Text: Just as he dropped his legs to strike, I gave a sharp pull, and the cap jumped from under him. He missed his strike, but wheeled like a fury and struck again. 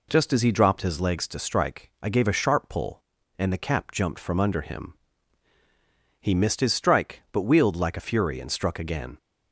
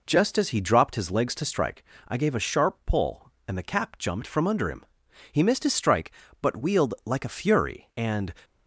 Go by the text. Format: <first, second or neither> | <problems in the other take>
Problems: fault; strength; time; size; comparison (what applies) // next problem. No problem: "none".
first | stops before "struck again"; at 8.4 s